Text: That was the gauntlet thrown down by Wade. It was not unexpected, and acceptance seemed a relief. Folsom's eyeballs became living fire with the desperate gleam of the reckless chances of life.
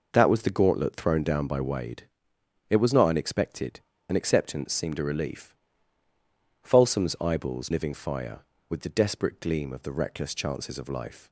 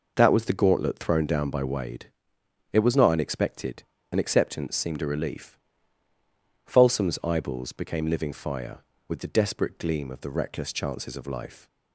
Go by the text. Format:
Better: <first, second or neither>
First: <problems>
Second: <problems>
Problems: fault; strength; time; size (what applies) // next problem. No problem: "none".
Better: second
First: skips "became"; at 7.7 s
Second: none